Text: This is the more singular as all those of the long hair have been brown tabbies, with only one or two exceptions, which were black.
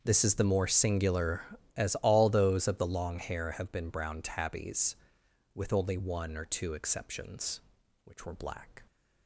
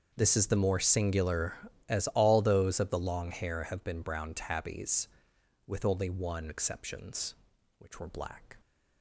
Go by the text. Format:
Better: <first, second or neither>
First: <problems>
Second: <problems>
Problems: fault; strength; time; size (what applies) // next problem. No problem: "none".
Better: first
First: starts louder than the rest; until 1.0 s; 6.5 dB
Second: starts louder than the rest; until 1.1 s; 6.5 dB // skips "or two"; at 6.4 s